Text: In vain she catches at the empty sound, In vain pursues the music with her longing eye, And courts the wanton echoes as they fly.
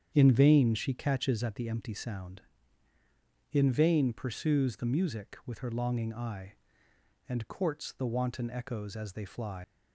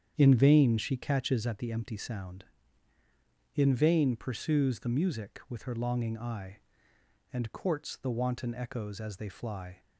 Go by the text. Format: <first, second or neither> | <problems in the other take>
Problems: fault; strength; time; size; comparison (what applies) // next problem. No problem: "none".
second | starts louder than the rest; strong; until 1.1 s; 8 dB; strong in the second // leaves "fly" unfinished; at 9.6 s; 115 ms